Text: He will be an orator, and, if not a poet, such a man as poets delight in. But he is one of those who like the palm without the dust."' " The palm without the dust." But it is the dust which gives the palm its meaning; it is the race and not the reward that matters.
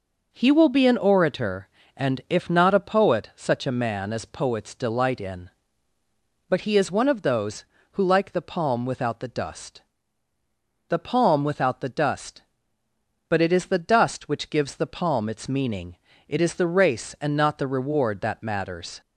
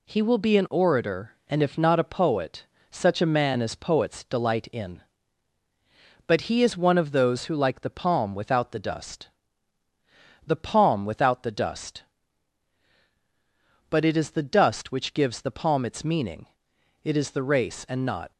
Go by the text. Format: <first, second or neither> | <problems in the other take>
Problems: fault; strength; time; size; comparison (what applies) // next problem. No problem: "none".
first | stops before "the reward that matters"; at 18.3 s